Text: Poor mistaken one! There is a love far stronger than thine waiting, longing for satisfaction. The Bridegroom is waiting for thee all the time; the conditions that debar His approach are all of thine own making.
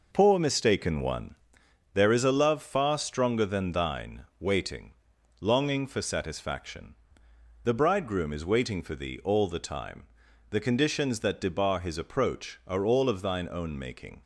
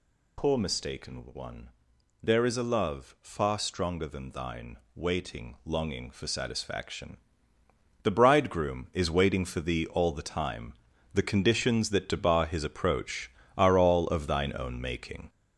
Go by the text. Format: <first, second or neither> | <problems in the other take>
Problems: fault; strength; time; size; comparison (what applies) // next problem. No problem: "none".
first | gets louder; noticeable; throughout; 5 dB // pauses between "thine" and "waiting"; slight; at 4.7 s; 0.18 s long